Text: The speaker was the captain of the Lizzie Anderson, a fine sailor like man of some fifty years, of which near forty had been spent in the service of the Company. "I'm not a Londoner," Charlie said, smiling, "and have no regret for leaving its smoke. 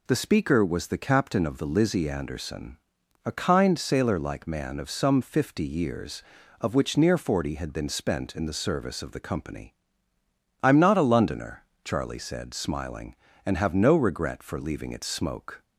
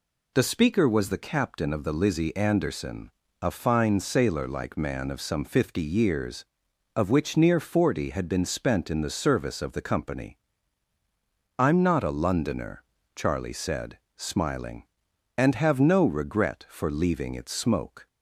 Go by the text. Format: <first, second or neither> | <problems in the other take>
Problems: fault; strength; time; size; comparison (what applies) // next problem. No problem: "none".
second | says "kind" for "fine"; at 3.3 s